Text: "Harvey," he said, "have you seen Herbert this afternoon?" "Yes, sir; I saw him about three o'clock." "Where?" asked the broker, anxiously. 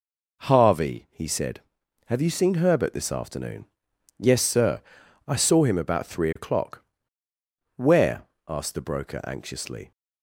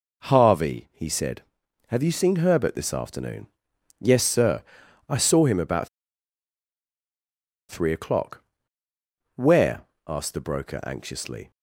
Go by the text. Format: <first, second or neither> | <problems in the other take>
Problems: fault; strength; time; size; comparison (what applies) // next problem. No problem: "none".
first | pauses between "about" and "three"; strong; at 5.8 s; 1.8 s long